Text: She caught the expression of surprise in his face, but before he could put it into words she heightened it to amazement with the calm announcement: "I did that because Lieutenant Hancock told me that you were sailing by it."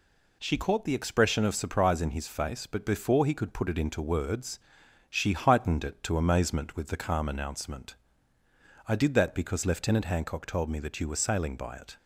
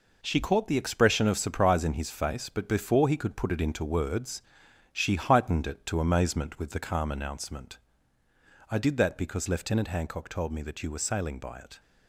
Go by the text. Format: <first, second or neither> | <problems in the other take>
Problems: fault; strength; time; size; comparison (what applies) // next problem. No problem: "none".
first | gets quieter; strong; throughout; 7.5 dB // pauses between "words" and "she"; noticeable; at 4.4 s; 0.52 s long; noticeable in the first